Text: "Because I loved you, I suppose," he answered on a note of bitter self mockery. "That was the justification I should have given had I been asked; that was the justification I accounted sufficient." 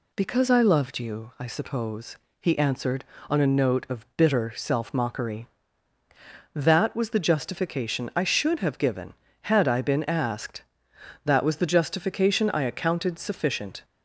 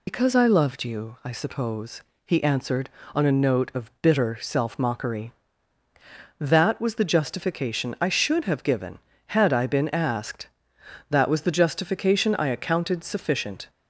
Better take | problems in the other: first | loses the start of "Because"; at 0.0 s; 75 ms

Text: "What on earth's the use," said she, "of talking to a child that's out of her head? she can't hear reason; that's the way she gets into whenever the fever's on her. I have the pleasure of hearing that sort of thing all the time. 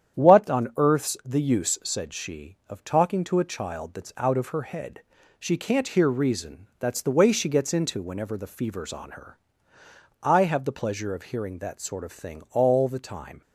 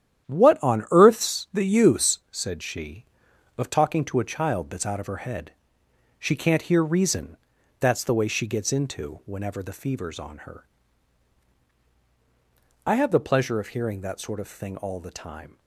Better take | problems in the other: neither | starts louder than the rest; strong; the same in both

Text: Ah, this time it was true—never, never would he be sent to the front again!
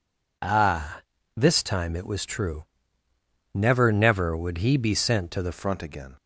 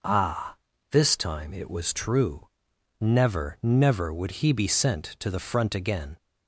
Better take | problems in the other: second | changes voice at "front"; from 5.5 s on; 0.6 s long

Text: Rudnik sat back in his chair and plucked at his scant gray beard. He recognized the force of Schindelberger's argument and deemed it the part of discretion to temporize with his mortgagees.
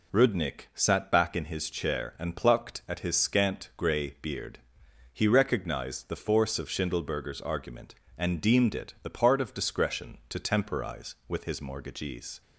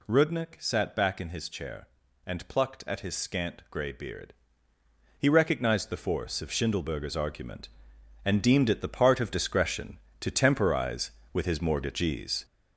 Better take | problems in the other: first | gets louder; noticeable; throughout; 6 dB

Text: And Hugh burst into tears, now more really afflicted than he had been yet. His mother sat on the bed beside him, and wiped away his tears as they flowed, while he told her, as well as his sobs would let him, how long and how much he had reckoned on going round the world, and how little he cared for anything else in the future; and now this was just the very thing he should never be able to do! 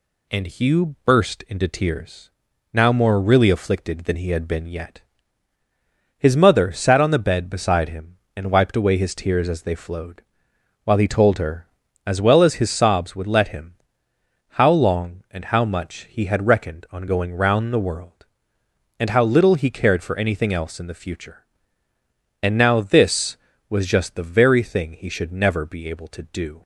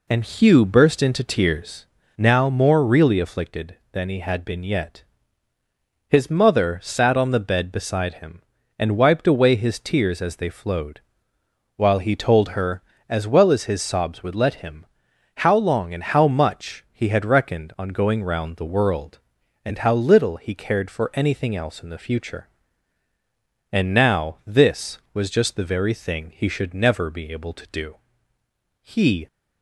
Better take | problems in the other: first | goes on to say "He"; slight; from 28.8 s on; 0.46 s long

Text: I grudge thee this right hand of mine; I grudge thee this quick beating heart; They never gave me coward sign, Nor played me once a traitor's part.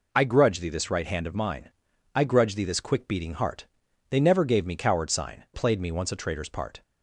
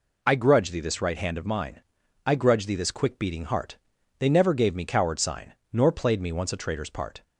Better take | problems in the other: second | skips "Nor"; at 5.4 s

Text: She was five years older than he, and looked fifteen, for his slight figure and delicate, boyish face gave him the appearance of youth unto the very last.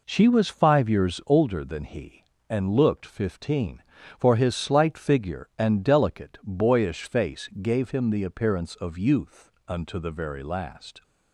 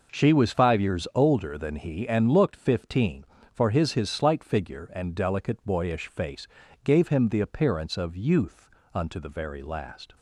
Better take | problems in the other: first | says "his" twice; at 3.9 s // pauses between "face" and "gave"; slight; at 6.4 s; 0.36 s long // pauses between "youth" and "unto"; slight; at 8.7 s; 0.24 s long; slight in the first

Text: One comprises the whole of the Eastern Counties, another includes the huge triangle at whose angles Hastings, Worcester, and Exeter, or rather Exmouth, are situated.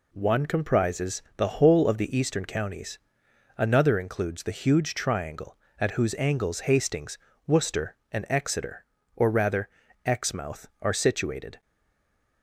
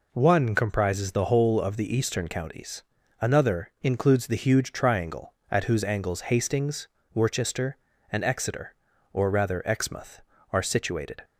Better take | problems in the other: second | pauses between "rather" and "Exmouth"; slight; at 9.6 s; 0.36 s long // stays silent after the last word; slight; from 11.6 s on; 0.8 s long

